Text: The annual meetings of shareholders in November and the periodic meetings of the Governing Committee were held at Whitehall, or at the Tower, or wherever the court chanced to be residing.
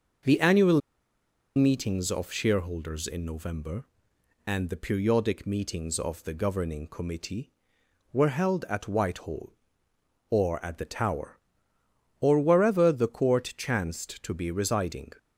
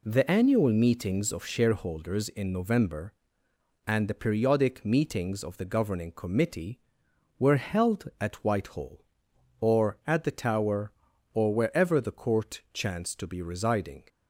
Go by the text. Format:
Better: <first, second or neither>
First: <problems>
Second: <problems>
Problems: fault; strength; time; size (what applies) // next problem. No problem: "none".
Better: second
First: starts louder than the rest; until 2.0 s; 6 dB // pauses between "annual" and "meetings"; noticeable; at 0.7 s; 0.75 s long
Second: none